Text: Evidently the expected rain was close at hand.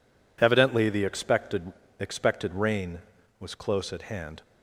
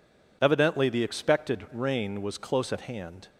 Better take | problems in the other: second | says "expected" twice; at 1.9 s

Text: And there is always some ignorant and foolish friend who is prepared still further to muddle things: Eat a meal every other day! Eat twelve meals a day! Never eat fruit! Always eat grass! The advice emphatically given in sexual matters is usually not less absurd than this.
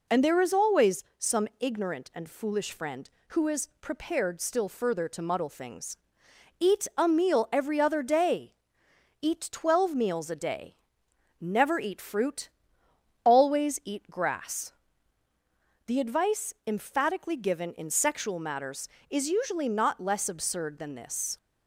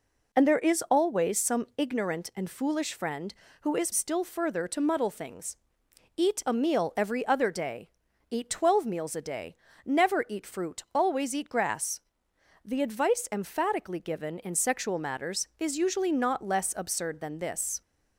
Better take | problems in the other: first | skips "prepared"; at 3.9 s

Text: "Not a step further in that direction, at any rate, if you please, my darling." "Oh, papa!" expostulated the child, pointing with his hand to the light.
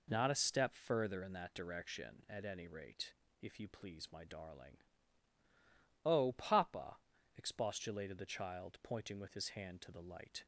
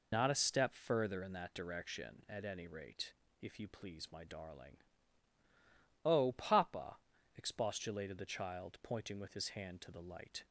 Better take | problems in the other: first | loses the start of "Not"; at 0.1 s; 45 ms

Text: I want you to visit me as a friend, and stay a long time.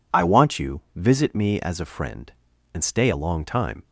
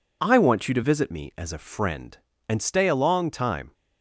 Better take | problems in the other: second | skips "to"; at 0.8 s

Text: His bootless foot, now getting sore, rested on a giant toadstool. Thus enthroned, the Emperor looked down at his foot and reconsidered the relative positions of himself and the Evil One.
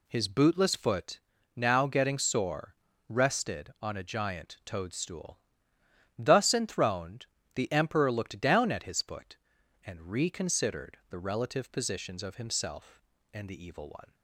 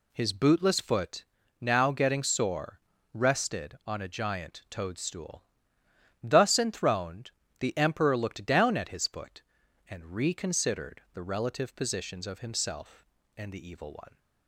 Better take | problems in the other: neither | none

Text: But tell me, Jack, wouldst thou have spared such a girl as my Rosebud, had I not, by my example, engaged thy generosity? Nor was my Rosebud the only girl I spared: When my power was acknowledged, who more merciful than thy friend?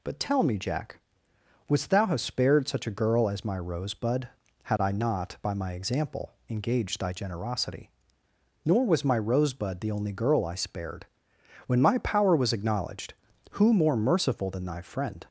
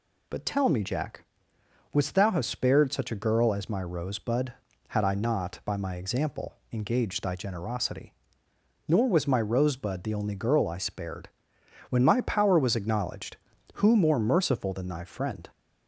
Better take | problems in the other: neither | none

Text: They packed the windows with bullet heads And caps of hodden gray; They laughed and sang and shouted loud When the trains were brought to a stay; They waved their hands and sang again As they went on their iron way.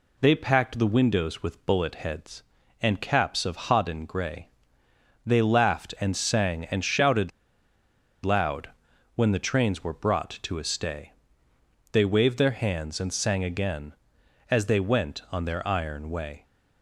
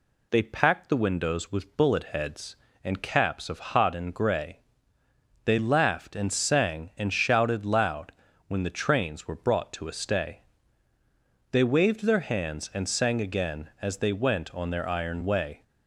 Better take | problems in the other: second | pauses between "shouted" and "loud"; noticeable; at 7.2 s; 0.93 s long // pauses between "loud" and "When"; noticeable; at 8.7 s; 0.46 s long; slight in the second

